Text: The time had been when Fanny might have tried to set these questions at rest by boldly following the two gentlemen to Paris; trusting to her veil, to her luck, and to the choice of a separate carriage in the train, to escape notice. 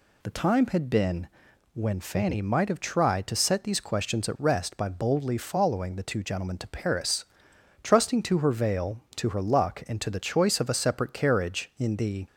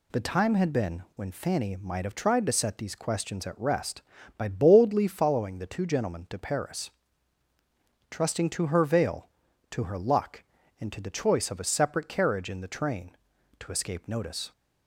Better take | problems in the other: second | pauses between "been" and "when"; at 1.2 s; 0.44 s long // stops before "train to escape notice"; at 12.2 s

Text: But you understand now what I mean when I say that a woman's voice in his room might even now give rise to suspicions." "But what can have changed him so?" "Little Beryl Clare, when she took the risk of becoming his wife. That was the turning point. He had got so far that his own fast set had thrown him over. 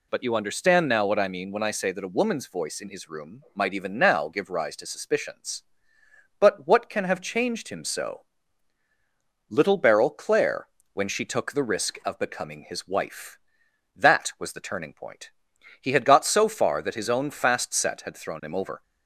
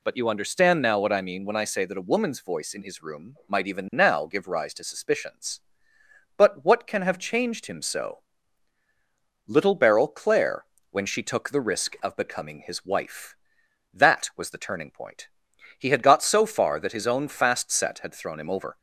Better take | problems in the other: neither | none

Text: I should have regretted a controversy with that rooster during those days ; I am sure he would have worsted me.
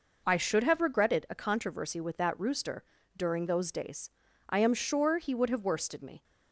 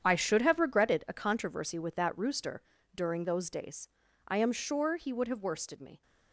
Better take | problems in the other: first | gets quieter; strong; throughout; 12 dB // pauses between "rooster" and "during"; slight; at 2.6 s; 0.32 s long; slight in the first

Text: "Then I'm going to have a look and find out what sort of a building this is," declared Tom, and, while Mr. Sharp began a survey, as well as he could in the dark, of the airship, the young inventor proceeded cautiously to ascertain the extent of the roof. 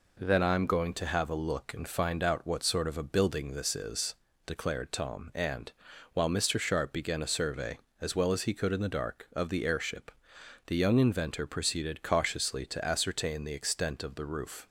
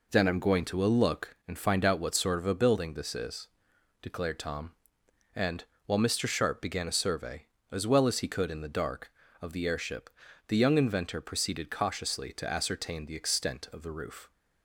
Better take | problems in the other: first | skips "have"; at 0.8 s

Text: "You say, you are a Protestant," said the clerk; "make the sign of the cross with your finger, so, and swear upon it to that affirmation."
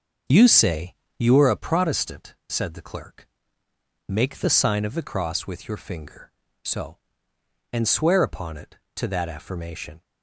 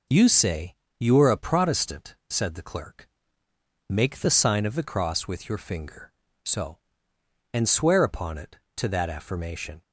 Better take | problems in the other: second | starts louder than the rest; until 1.4 s; 6.5 dB

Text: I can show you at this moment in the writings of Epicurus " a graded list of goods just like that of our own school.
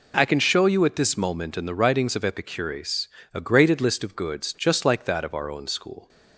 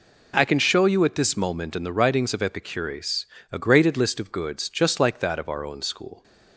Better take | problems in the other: neither | none

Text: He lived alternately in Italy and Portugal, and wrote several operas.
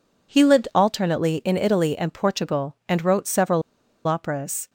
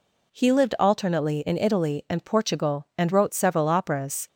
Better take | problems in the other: second | pauses between "several" and "operas"; noticeable; at 3.6 s; 0.46 s long

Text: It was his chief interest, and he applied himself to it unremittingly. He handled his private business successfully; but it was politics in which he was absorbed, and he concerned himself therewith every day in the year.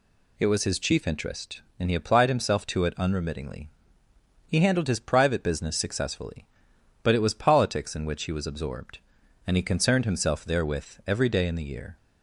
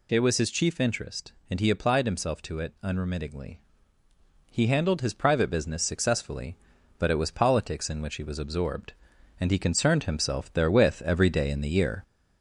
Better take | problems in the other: first | gets louder; slight; throughout; 2.5 dB

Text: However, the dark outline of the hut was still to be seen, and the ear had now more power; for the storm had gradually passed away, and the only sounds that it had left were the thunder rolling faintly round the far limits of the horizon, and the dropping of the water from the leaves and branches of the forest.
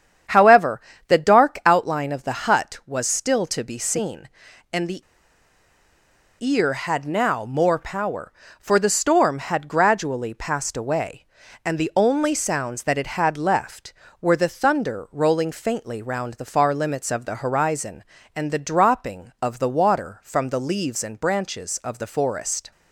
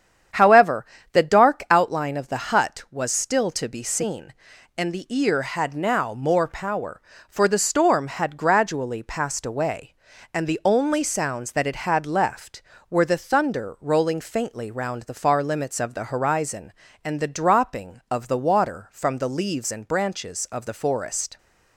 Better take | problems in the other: second | starts louder than the rest; strong; until 1.5 s; 8.5 dB; strong in the second // pauses between "the" and "ear"; strong; at 5.0 s; 1.3 s long

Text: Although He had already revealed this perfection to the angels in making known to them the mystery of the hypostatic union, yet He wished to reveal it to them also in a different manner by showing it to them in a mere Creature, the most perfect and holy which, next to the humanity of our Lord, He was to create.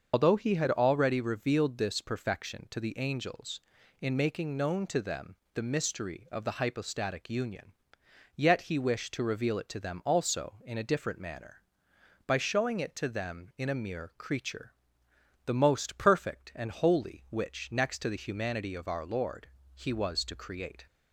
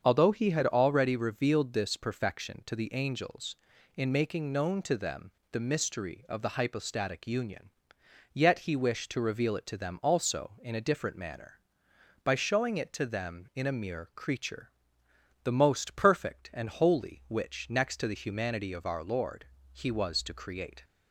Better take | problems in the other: second | loses the start of "Although"; at 0.1 s; 50 ms // starts louder than the rest; until 1.1 s; 6.5 dB; also in the second // pauses between "them" and "the"; slight; at 5.3 s; 0.20 s long; slight in the second

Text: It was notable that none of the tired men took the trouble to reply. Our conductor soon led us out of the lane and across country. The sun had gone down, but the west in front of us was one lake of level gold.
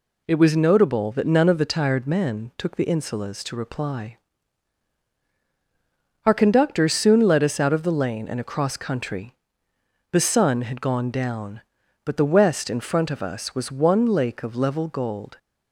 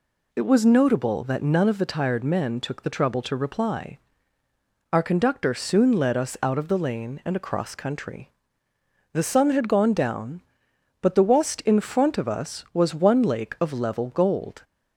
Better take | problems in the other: second | says "insulas" for "trouble"; at 2.8 s

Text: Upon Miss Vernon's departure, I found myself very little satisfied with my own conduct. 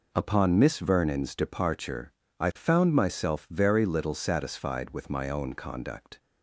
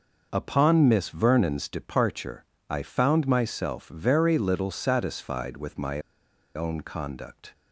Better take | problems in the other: first | pauses between "my" and "own"; noticeable; at 5.9 s; 0.55 s long

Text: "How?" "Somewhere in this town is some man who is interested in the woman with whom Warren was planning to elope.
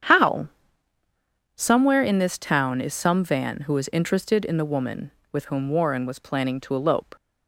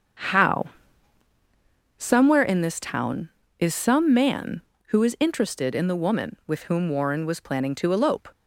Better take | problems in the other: second | starts louder than the rest; strong; until 2.1 s; 8.5 dB; strong in the second // says "van" for "man"; at 3.2 s

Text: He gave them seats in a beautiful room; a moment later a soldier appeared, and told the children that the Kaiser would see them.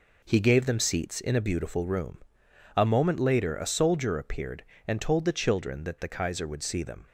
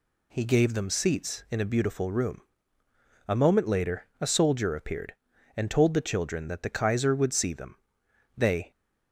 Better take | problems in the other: first | pauses between "later" and "a"; slight; at 4.0 s; 0.15 s long // goes on to say "They"; slight; from 8.3 s on; 0.34 s long

